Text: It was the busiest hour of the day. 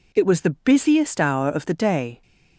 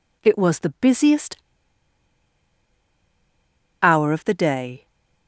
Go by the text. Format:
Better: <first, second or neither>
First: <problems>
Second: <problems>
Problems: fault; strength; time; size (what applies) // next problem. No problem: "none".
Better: first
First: none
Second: pauses between "busiest" and "hour"; strong; at 1.3 s; 2.4 s long